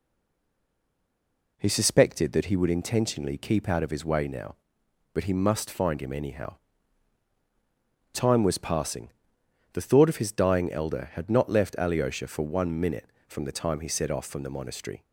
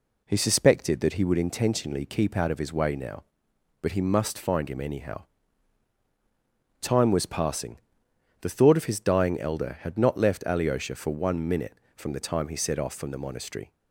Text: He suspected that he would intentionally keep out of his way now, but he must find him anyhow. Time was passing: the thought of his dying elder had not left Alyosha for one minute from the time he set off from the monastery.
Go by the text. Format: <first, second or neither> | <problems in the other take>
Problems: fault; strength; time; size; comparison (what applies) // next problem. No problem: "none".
second | stays silent before the first word; noticeable; until 1.5 s; 1.5 s long